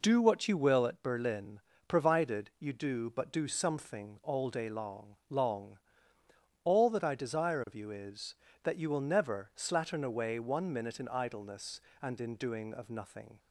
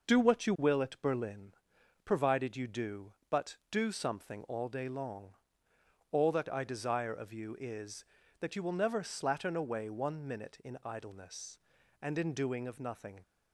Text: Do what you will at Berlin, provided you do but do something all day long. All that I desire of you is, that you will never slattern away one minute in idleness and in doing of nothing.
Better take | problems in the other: second | says "long" twice; at 5.2 s

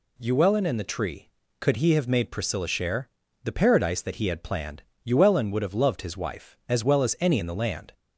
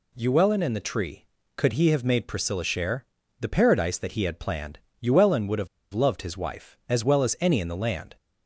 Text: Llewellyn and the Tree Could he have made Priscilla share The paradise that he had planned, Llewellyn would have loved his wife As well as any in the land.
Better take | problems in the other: first | pauses between "share" and "The"; slight; at 3.0 s; 0.34 s long; slight in the first // pauses between "have" and "loved"; slight; at 5.6 s; 0.26 s long

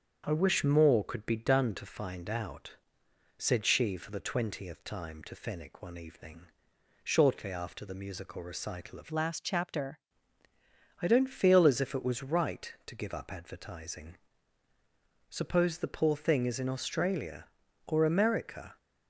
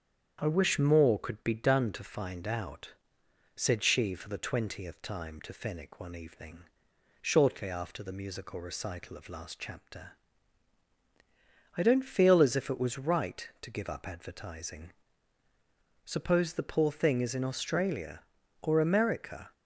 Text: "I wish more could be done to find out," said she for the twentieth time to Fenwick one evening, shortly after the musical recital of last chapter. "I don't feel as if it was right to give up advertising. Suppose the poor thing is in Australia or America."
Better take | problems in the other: second | starts louder than the rest; strong; until 1.2 s; 7.5 dB; strong in the second // changes voice from "last" to "chapter"; from 9.1 to 9.9 s; 0.8 s long

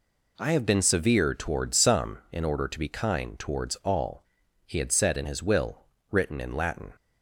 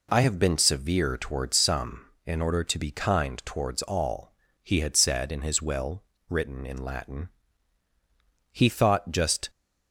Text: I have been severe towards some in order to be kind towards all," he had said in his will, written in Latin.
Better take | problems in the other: first | goes on to say "He thought just"; noticeable; from 8.5 s on; 0.98 s long

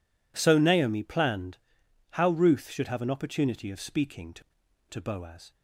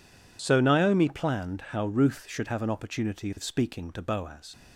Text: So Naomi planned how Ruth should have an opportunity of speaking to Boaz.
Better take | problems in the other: second | pauses between "planned" and "how"; noticeable; at 1.5 s; 0.52 s long // says "to" twice; at 4.8 s

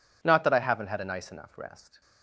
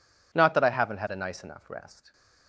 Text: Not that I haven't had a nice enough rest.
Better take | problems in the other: neither | none

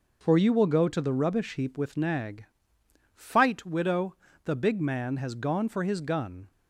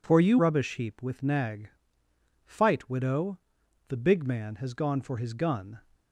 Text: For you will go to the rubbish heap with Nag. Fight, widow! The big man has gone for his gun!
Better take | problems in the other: first | skips "will go to the"; at 0.3 s

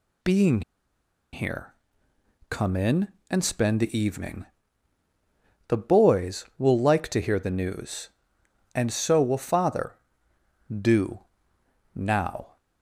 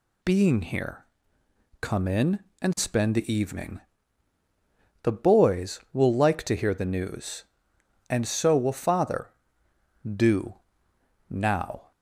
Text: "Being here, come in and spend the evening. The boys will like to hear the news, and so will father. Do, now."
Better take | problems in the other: second | pauses between "Being" and "here"; noticeable; at 0.6 s; 0.71 s long

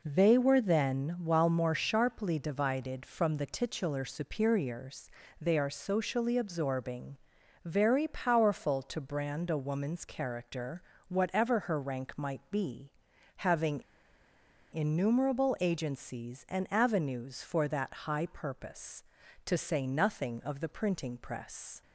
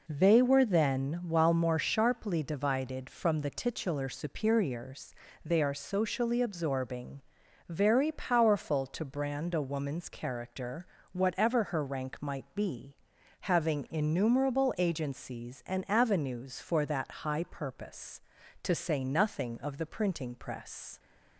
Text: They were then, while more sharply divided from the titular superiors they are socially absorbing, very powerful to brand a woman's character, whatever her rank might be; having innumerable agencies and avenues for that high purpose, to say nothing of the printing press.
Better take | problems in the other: second | pauses between "superiors" and "they"; slight; at 5.0 s; 0.32 s long; slight in the second // pauses between "having" and "innumerable"; noticeable; at 13.8 s; 0.93 s long

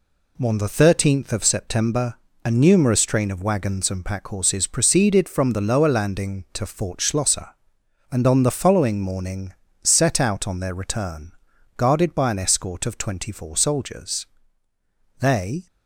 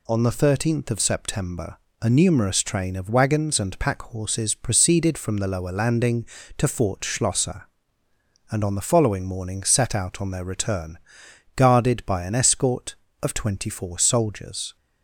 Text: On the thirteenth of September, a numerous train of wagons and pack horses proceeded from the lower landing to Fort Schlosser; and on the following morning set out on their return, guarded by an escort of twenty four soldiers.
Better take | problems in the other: second | pauses between "morning" and "set"; slight; at 9.5 s; 0.30 s long // goes on to say "They"; slight; from 15.2 s on; 0.46 s long

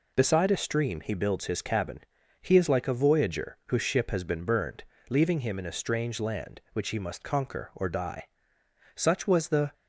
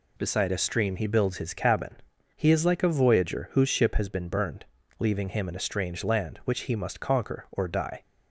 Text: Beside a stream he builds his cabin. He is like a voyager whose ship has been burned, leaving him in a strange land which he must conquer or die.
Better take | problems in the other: second | goes on to say "Such was the"; noticeable; from 8.9 s on; 0.78 s long

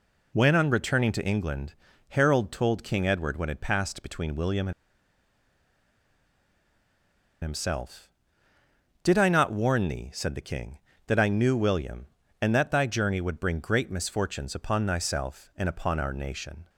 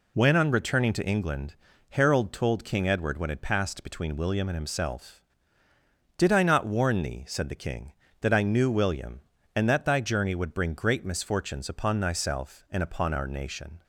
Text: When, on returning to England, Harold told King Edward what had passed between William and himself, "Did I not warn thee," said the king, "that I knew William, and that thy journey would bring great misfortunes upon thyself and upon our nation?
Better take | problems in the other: second | pauses between "and" and "himself"; strong; at 4.7 s; 2.6 s long

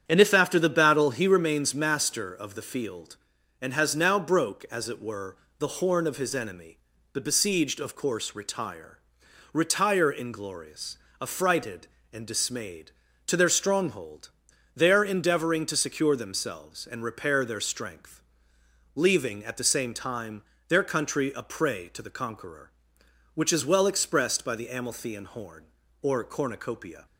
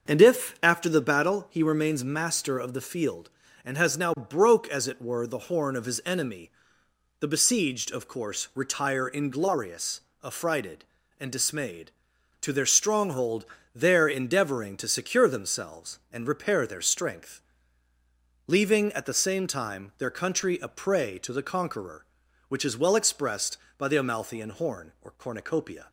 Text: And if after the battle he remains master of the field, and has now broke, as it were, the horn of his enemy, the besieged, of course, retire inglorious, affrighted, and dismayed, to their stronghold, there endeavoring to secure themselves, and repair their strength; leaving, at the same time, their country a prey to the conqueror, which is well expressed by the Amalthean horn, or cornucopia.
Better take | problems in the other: second | starts louder than the rest; strong; until 1.0 s; 8.5 dB; also in the second // says "retire" twice; at 9.5 s

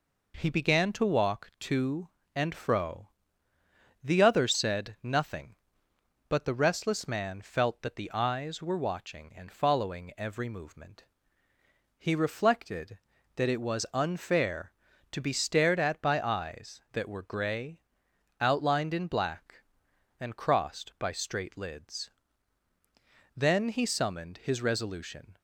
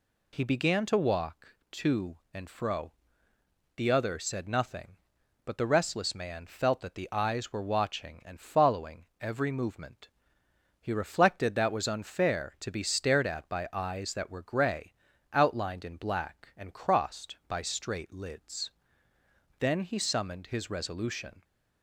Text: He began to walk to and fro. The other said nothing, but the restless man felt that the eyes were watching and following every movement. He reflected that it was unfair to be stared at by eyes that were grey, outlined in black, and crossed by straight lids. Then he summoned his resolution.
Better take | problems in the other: first | pauses between "following" and "every"; slight; at 9.0 s; 0.16 s long // skips "it"; at 11.6 s

